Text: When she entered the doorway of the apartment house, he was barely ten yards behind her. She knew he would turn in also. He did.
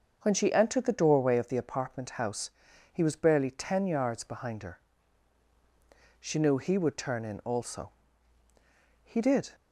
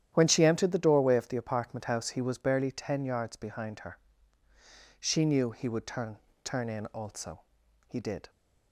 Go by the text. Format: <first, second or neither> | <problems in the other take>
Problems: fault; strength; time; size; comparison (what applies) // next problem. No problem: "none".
first | starts louder than the rest; strong; until 1.1 s; 10.5 dB; also in the first // says "turn" twice; at 6.4 s